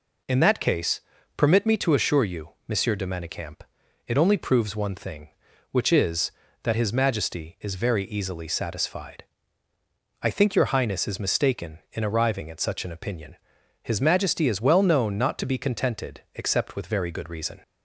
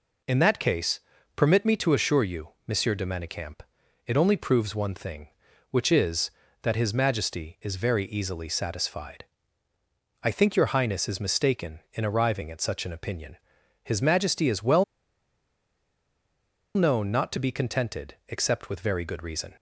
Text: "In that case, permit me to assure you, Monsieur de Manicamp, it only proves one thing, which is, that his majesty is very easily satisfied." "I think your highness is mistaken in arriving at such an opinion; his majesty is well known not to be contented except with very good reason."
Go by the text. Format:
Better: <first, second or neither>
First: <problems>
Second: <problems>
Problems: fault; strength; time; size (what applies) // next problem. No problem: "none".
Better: first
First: none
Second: pauses between "well" and "known"; strong; at 14.8 s; 1.9 s long